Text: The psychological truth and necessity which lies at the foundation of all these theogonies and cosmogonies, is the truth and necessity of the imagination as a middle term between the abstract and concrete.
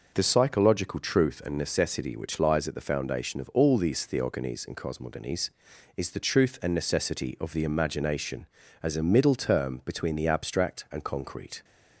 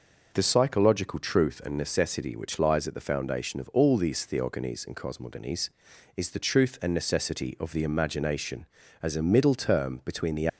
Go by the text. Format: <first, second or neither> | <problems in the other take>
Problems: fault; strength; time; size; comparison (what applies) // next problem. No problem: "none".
first | stops before "abstract and concrete"; at 10.4 s